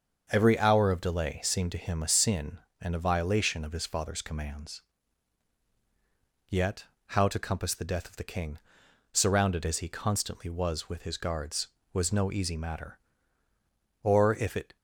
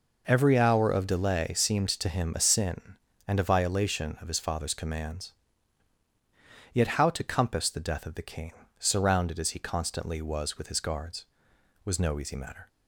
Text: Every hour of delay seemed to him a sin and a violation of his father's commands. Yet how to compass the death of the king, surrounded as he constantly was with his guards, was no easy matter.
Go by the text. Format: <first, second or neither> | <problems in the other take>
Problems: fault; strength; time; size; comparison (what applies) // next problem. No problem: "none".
second | starts louder than the rest; until 1.3 s; 6.5 dB // pauses between "Yet" and "how"; slight; at 6.8 s; 0.24 s long // goes on to say "Or if it"; noticeable; from 14.0 s on; 0.74 s long